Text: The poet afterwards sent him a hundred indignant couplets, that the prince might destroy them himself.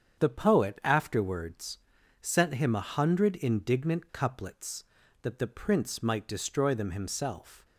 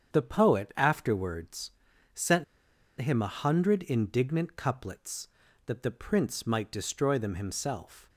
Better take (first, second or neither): first